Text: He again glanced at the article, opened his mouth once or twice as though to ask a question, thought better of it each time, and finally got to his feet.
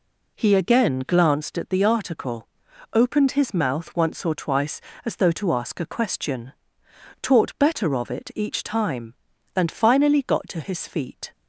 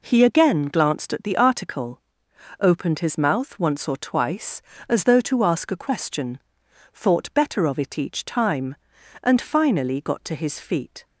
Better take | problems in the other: second | says "taught" for "thought"; at 7.2 s

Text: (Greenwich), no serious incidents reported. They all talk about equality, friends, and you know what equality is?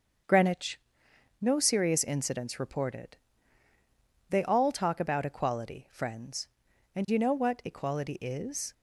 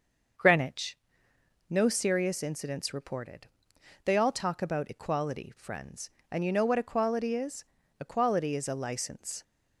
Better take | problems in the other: first | starts louder than the rest; until 2.1 s; 6 dB; also in the first // goes on to say "Equality is a license"; from 7.9 s on; 1.4 s long

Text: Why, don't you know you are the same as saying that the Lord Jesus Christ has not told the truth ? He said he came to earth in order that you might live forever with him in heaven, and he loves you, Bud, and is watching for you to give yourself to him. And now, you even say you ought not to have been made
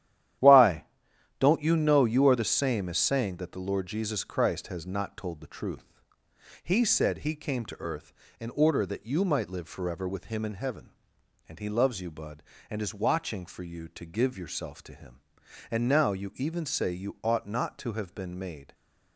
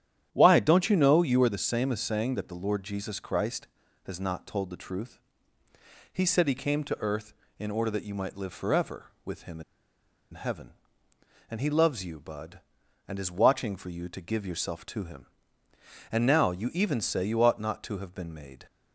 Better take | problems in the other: first | starts louder than the rest; strong; until 1.3 s; 10.5 dB; strong in the first // pauses between "in" and "heaven"; noticeable; at 9.6 s; 0.70 s long

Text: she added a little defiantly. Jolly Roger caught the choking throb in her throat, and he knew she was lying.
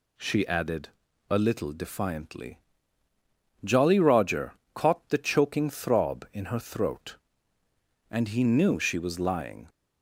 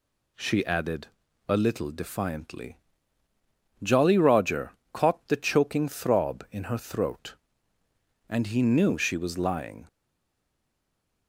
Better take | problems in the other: first | pauses between "added" and "a"; at 1.0 s; 0.40 s long; also in the first // pauses between "Roger" and "caught"; slight; at 4.7 s; 0.22 s long; slight in the first // stays silent after the last word; noticeable; from 9.8 s on; 1.4 s long

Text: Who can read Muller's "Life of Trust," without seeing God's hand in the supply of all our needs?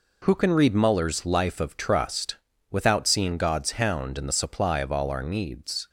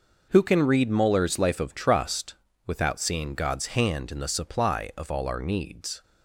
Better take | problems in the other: second | says "hound" for "hand"; at 3.7 s

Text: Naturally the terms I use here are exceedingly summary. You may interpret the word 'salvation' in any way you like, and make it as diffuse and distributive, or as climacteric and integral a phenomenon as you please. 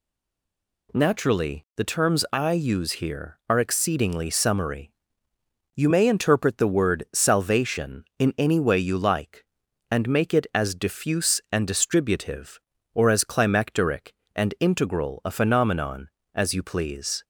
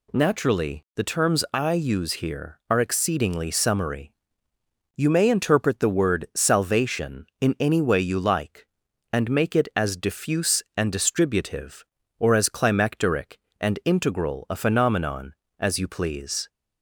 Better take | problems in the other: second | stays silent before the first word; slight; until 0.8 s; 0.8 s long

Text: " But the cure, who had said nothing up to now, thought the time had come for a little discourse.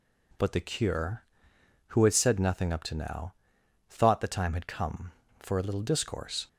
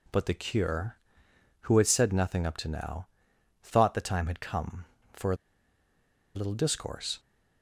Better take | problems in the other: first | pauses between "a" and "little"; at 5.3 s; 0.99 s long

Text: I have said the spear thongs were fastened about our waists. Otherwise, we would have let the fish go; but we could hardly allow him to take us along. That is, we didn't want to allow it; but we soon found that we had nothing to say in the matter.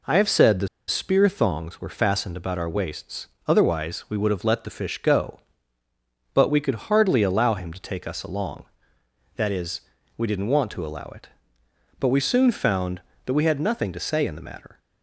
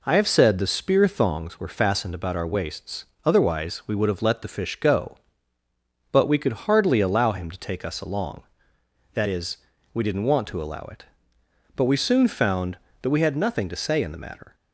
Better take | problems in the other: second | pauses between "the" and "spear"; slight; at 0.6 s; 0.21 s long

